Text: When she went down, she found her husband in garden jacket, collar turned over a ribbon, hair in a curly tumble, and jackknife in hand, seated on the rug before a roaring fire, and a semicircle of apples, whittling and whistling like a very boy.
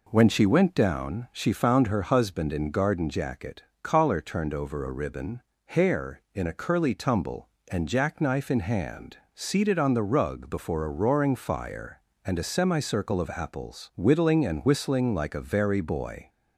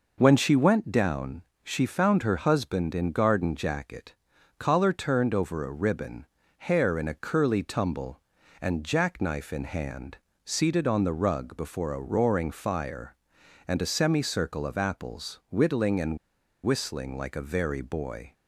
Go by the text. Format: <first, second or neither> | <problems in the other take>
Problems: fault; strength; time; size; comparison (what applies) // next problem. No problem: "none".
first | pauses between "and" and "whistling"; noticeable; at 16.1 s; 0.47 s long